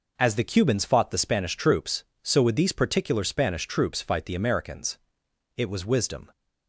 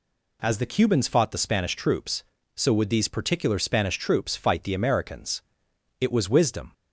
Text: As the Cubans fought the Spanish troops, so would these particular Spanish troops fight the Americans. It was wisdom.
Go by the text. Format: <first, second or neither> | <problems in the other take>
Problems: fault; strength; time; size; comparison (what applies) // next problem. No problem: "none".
neither | none